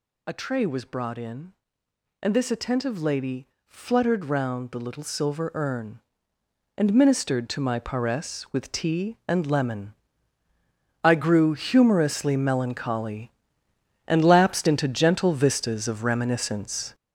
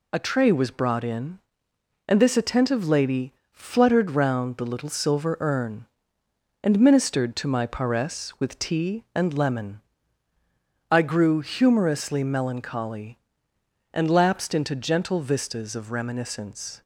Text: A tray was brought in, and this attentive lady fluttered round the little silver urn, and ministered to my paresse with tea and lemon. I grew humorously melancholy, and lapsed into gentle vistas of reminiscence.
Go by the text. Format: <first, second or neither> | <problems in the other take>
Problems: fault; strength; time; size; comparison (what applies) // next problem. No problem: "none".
second | gets louder; strong; throughout; 7.5 dB // pauses between "lady" and "fluttered"; slight; at 3.4 s; 0.18 s long; slight in the second